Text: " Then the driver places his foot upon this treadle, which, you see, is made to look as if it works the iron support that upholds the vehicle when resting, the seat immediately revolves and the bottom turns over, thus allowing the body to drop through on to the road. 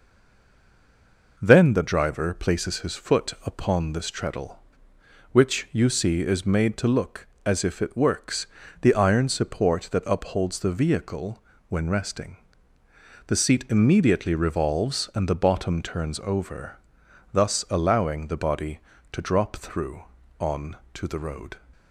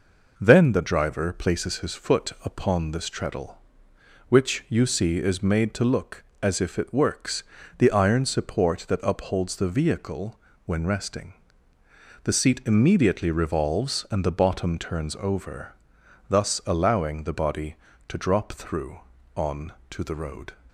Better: second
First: stays silent before the first word; noticeable; until 1.3 s; 1.3 s long // pauses between "works" and "the"; slight; at 8.4 s; 0.34 s long // pauses between "vehicle" and "when"; slight; at 11.4 s; 0.28 s long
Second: pauses between "works" and "the"; slight; at 7.4 s; 0.34 s long // pauses between "vehicle" and "when"; slight; at 10.3 s; 0.28 s long

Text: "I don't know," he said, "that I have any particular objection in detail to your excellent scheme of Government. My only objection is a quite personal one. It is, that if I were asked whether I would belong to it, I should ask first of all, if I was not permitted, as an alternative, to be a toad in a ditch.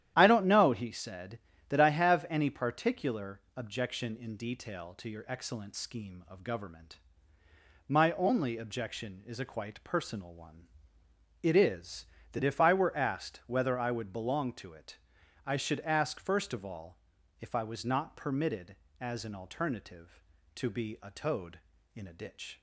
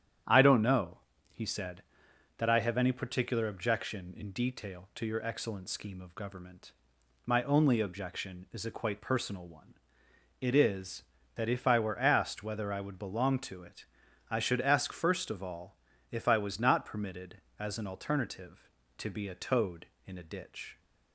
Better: neither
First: starts louder than the rest; strong; until 1.1 s; 11 dB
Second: starts louder than the rest; strong; until 1.5 s; 9.5 dB

